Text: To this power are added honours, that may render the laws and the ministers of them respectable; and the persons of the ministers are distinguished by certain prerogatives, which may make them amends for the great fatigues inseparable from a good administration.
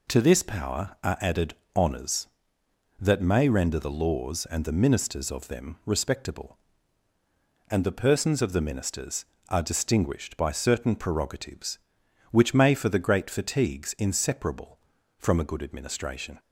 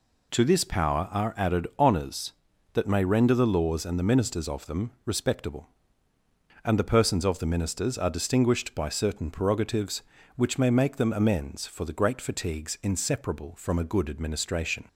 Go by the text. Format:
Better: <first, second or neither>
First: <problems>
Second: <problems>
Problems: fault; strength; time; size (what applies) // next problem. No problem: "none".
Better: second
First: pauses between "added" and "honours"; slight; at 1.5 s; 0.22 s long // skips "make them amends"; at 12.7 s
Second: none